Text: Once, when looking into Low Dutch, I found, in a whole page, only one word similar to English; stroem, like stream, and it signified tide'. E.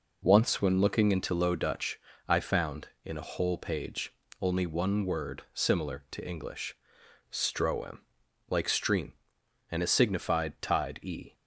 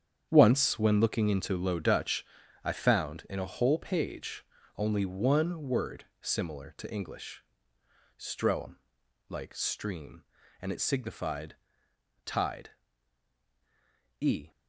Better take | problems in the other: first | gets quieter; strong; throughout; 11.5 dB // pauses between "word" and "similar"; slight; at 6.0 s; 0.18 s long // pauses between "signified" and "tide"; noticeable; at 11.5 s; 0.70 s long

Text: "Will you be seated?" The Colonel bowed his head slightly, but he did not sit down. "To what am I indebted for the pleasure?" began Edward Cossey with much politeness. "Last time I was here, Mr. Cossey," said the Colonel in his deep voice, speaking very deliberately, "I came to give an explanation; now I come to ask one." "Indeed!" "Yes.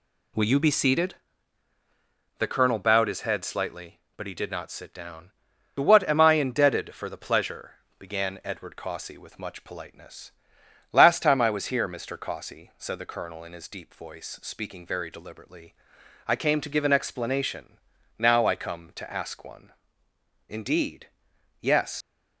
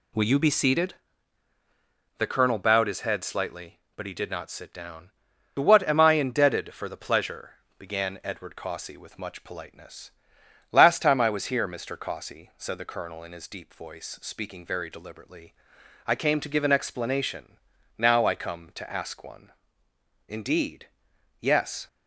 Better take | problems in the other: second | leaves "Yes" unfinished; at 22.0 s; 70 ms

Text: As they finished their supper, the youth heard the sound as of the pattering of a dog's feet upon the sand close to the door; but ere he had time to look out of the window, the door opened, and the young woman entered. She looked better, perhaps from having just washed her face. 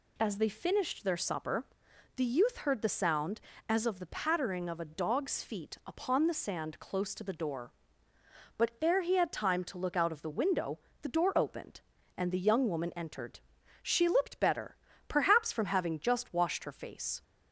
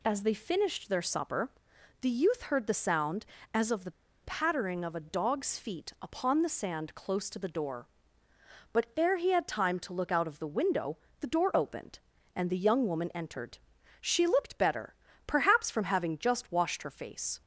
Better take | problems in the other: first | pauses between "the" and "pattering"; slight; at 3.9 s; 0.32 s long

